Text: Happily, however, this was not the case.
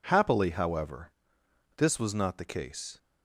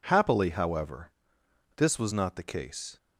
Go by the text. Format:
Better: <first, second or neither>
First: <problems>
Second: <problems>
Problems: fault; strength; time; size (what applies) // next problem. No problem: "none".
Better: neither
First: none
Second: none